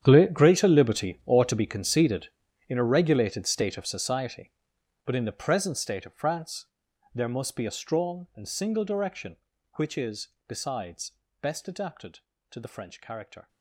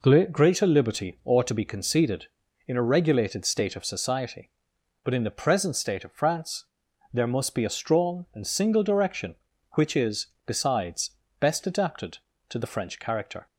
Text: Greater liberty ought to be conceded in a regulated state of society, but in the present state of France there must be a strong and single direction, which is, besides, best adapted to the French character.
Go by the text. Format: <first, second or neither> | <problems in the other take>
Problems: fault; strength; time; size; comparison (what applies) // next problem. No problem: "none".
second | gets quieter; strong; throughout; 16.5 dB // pauses between "France" and "there"; noticeable; at 6.6 s; 0.48 s long; noticeable in the second